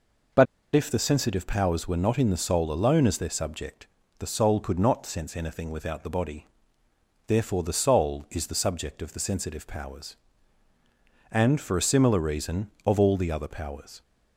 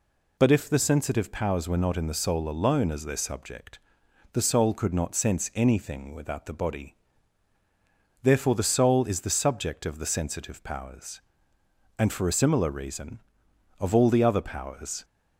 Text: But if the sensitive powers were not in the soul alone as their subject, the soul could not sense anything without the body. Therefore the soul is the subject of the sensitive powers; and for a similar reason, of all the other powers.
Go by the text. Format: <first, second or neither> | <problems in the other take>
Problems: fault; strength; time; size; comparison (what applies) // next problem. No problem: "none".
second | pauses between "But" and "if"; slight; at 0.4 s; 0.30 s long